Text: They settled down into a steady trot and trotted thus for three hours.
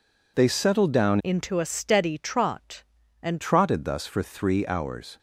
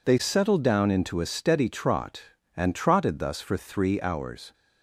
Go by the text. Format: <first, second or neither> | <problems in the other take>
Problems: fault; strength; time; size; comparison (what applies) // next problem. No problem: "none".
second | changes voice from "into" to "and"; from 1.2 to 3.4 s; 2.2 s long